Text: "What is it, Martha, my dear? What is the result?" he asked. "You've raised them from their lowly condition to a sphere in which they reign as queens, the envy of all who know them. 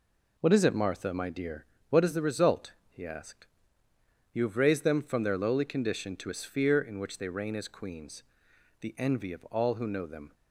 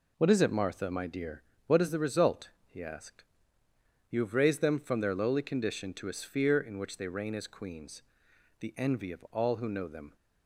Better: neither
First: none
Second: none

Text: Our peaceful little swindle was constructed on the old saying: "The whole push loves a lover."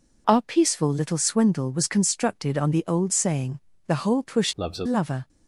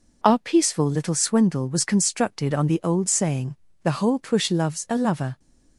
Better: second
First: changes voice from "loves" to "a"; from 4.5 to 4.8 s; 0.3 s long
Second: none

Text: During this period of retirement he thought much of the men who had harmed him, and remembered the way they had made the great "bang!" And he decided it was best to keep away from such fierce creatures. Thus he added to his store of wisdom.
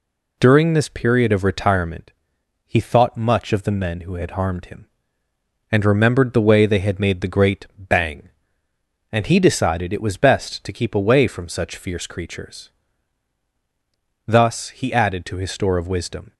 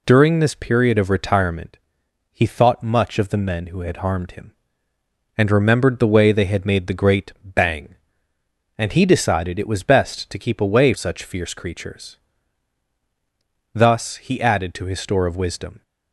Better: first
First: pauses between "retirement" and "he"; noticeable; at 2.1 s; 0.54 s long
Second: pauses between "retirement" and "he"; noticeable; at 1.7 s; 0.54 s long // skips "from"; at 10.9 s

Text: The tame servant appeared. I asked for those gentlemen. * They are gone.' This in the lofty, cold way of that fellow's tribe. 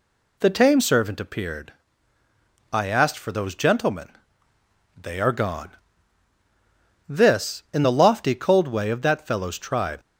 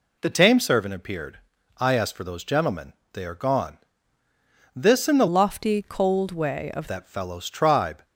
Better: first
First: none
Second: changes voice from "lofty" to "of"; from 5.2 to 6.8 s; 1.6 s long

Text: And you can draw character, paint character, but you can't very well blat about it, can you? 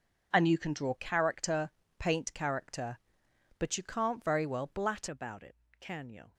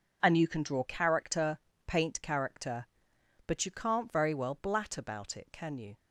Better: second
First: changes voice at "about"; from 5.0 s on; 1.3 s long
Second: none

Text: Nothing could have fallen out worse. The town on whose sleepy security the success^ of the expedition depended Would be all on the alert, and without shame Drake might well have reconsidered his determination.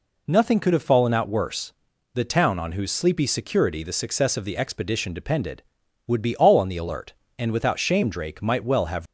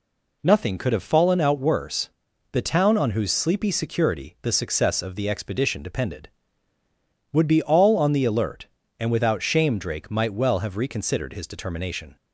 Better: second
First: stops before "reconsidered his determination"; at 9.0 s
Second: none

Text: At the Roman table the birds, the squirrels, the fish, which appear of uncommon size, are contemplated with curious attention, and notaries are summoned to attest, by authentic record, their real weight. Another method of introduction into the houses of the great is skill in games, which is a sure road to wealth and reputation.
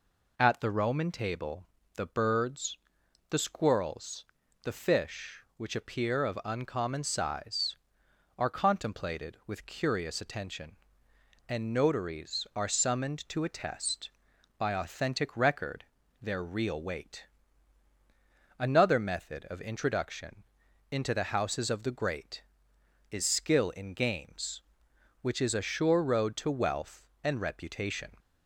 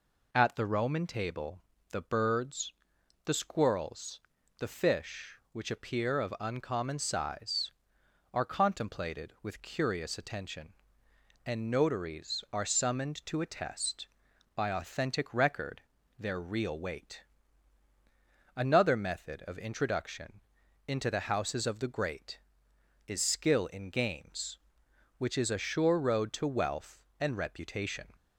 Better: neither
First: pauses between "table" and "the"; slight; at 1.6 s; 0.28 s long // pauses between "introduction" and "into"; noticeable; at 20.4 s; 0.48 s long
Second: pauses between "table" and "the"; slight; at 1.6 s; 0.28 s long // pauses between "introduction" and "into"; noticeable; at 20.3 s; 0.47 s long

